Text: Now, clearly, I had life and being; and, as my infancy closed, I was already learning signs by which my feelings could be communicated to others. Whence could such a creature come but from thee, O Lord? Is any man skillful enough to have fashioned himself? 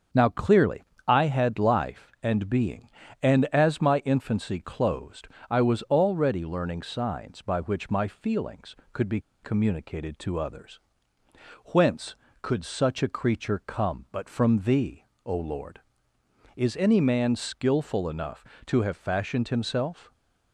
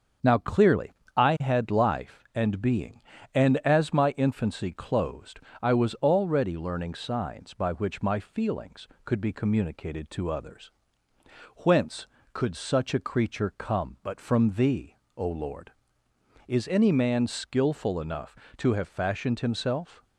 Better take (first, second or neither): second